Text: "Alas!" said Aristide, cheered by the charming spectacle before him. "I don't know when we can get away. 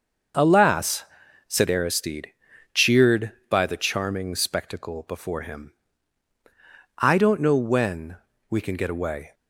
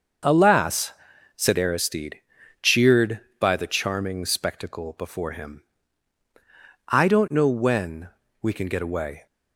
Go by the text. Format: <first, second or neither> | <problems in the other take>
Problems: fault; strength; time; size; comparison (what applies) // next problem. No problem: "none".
neither | starts louder than the rest; the same in both // pauses between "when" and "we"; slight; the same in both